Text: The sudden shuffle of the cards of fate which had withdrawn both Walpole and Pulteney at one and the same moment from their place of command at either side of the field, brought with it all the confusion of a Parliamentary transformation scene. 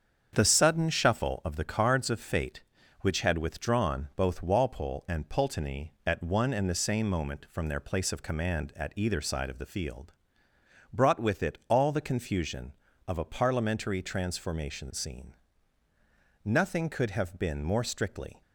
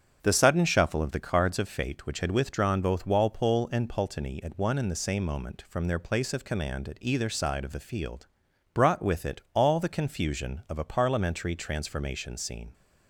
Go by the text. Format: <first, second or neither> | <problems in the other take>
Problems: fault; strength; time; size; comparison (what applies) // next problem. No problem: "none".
second | starts louder than the rest; strong; until 1.3 s; 7.5 dB; strong in the second // goes on to say "Nothing could have been more strictly"; strong; from 16.4 s on; 1.9 s long